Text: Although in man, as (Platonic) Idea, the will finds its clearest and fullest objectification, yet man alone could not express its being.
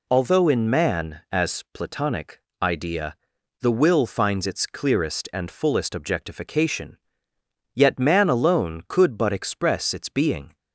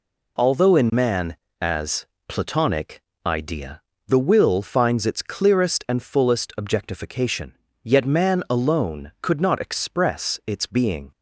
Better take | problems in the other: second | says "but" for "not"; at 9.1 s

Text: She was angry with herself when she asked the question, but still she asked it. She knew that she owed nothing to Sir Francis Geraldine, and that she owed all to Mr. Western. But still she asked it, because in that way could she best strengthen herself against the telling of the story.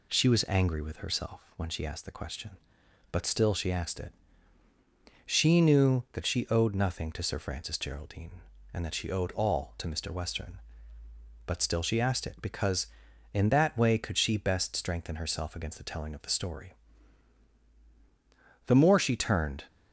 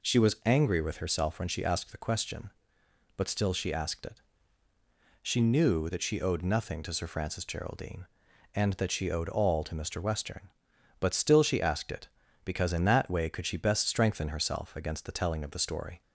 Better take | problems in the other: second | goes on to say "The more she turned"; noticeable; from 18.6 s on; 1.0 s long

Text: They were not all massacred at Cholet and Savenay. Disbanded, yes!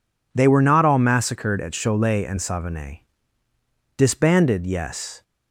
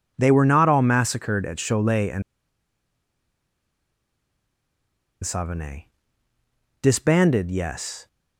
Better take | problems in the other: first | pauses between "and" and "Savenay"; strong; at 2.2 s; 3.0 s long

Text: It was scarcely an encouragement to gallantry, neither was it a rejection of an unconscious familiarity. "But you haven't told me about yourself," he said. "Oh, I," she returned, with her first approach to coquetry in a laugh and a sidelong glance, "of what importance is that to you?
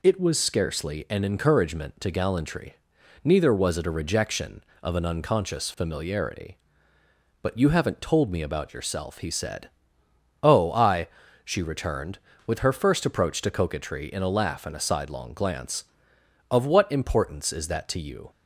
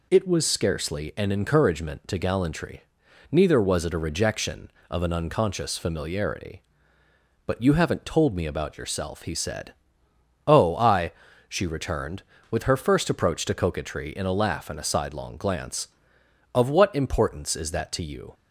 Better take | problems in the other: neither | none

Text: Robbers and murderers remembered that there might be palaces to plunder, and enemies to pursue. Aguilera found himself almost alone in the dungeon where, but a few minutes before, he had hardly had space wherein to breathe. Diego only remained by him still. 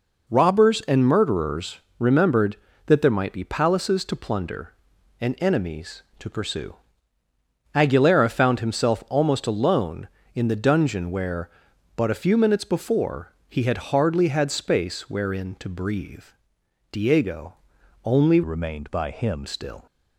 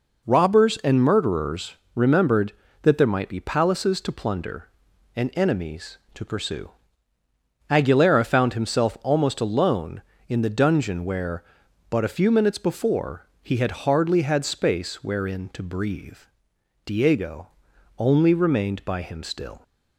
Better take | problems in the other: second | pauses between "murderers" and "remembered"; slight; at 1.7 s; 0.20 s long; slight in the second // pauses between "Diego" and "only"; noticeable; at 17.5 s; 0.50 s long; noticeable in the second // changes voice from "remained" to "him"; from 18.4 to 19.4 s; 1.0 s long

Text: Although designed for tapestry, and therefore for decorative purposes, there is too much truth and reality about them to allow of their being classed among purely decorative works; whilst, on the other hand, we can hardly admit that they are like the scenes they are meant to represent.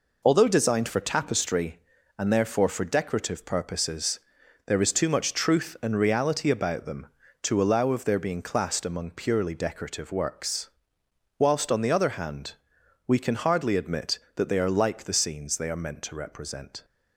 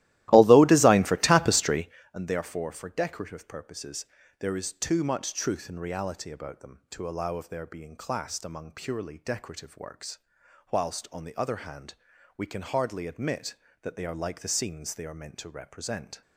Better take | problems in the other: first | starts louder than the rest; strong; until 2.1 s; 16 dB

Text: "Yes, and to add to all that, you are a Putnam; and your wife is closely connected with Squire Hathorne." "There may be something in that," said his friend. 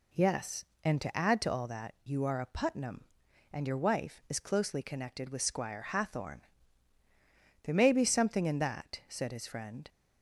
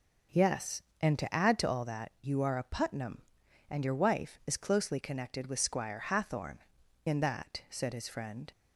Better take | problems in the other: first | skips "There may be something"; at 6.8 s

